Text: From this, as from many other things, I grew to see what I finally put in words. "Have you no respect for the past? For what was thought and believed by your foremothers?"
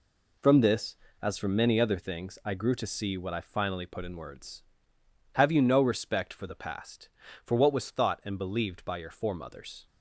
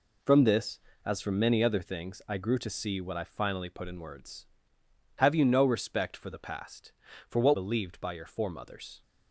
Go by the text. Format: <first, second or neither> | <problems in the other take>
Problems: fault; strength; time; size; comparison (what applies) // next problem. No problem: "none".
first | skips "was thought and"; at 7.5 s